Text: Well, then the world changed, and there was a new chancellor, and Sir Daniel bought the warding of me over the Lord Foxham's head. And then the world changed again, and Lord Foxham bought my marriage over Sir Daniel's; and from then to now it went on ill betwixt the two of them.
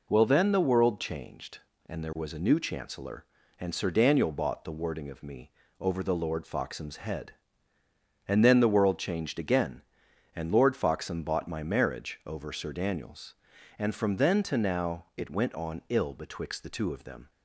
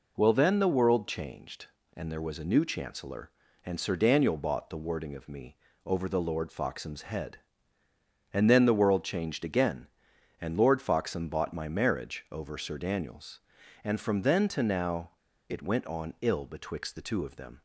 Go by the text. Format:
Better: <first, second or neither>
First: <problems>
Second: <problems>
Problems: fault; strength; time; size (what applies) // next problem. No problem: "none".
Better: first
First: pauses between "me" and "over"; slight; at 5.4 s; 0.30 s long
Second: pauses between "me" and "over"; slight; at 5.5 s; 0.30 s long // pauses between "now" and "it"; at 15.1 s; 0.36 s long